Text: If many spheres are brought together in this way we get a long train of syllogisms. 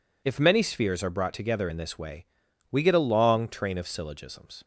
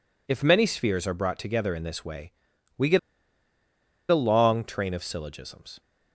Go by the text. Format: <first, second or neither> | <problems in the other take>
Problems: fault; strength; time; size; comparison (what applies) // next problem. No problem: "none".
first | pauses between "way" and "we"; noticeable; at 2.3 s; 0.46 s long; noticeable in the first // pauses between "get" and "a"; at 2.9 s; 1.1 s long